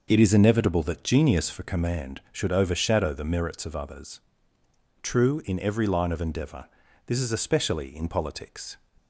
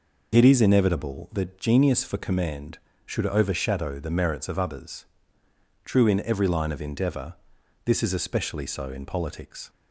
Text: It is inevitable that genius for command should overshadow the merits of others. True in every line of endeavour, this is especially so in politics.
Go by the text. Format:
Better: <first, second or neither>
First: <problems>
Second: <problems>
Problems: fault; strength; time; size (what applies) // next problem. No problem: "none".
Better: second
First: skips "so"; at 7.9 s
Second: none